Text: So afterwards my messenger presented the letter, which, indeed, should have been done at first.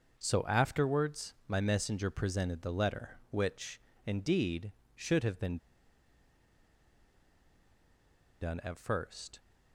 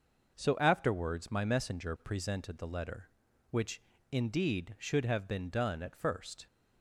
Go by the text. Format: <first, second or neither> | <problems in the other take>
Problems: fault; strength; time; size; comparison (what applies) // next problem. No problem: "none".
second | starts louder than the rest; until 1.2 s; 6 dB // pauses between "been" and "done"; strong; at 5.5 s; 2.8 s long